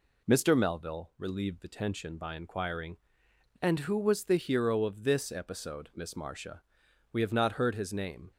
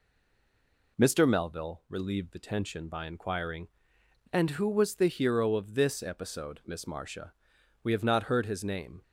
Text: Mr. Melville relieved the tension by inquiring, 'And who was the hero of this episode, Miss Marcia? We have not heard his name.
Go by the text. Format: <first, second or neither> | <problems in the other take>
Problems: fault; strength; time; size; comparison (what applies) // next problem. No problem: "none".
first | stays silent before the first word; slight; until 0.9 s; 0.9 s long